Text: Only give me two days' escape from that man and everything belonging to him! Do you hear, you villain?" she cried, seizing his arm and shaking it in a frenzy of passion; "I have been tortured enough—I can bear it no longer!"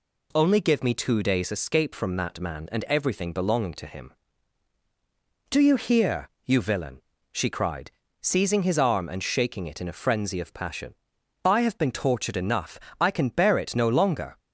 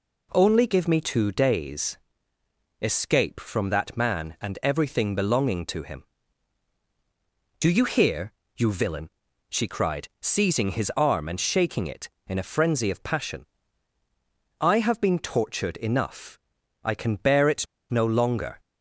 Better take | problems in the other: first | pauses between "days" and "escape"; noticeable; at 1.9 s; 0.82 s long // pauses between "it" and "no"; slight; at 17.6 s; 0.24 s long

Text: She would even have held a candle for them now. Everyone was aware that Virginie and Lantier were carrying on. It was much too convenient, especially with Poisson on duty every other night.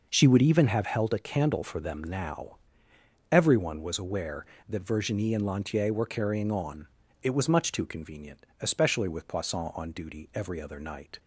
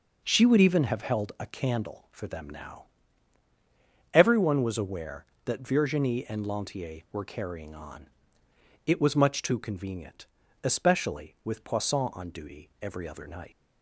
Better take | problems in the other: first | leaves "night" unfinished; at 13.5 s; 120 ms

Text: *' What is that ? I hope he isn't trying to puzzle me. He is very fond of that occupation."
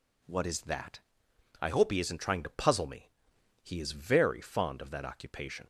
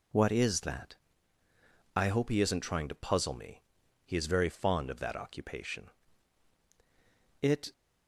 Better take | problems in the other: first | goes on to say "It"; slight; from 7.4 s on; 0.32 s long

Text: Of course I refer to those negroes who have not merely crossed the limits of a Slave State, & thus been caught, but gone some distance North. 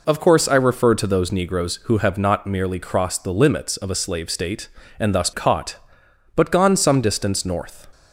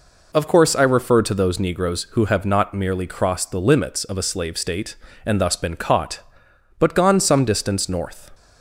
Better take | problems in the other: second | skips "been"; at 5.3 s

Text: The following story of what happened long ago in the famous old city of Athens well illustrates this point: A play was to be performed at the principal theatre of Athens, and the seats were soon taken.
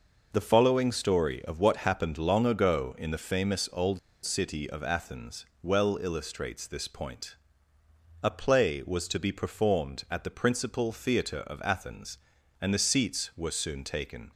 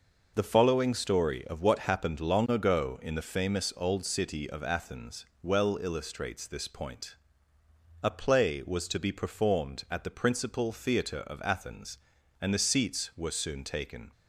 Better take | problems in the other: second | pauses between "old" and "city"; slight; at 3.9 s; 0.26 s long // pauses between "Athens" and "well"; slight; at 5.4 s; 0.18 s long; slight in the second

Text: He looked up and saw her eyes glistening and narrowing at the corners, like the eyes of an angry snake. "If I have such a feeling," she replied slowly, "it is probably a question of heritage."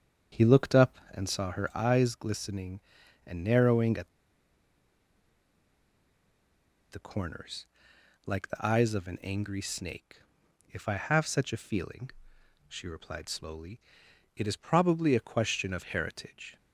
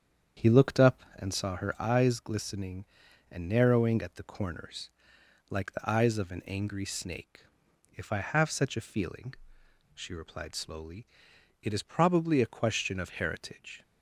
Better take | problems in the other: second | starts louder than the rest; strong; until 1.4 s; 8 dB; strong in the second // pauses between "at" and "the"; strong; at 4.0 s; 2.8 s long

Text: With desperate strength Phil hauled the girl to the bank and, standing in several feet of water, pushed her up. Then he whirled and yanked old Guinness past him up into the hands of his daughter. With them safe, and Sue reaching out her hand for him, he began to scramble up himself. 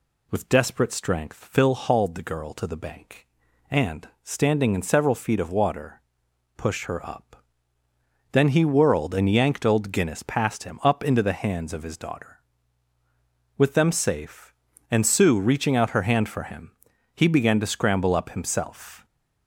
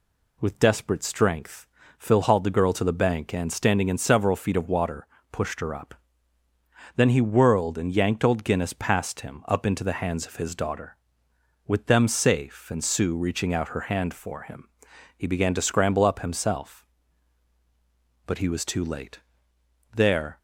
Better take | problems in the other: first | pauses between "strength" and "Phil"; slight; at 1.6 s; 0.32 s long // goes on to say "But he was too late There"; strong; from 18.2 s on; 2.1 s long

